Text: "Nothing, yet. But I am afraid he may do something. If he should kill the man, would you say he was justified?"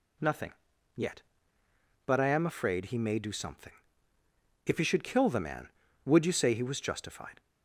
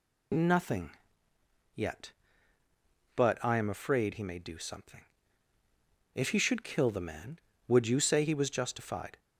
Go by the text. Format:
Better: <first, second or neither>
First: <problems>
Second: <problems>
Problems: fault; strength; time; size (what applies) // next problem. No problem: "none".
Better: neither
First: none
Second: none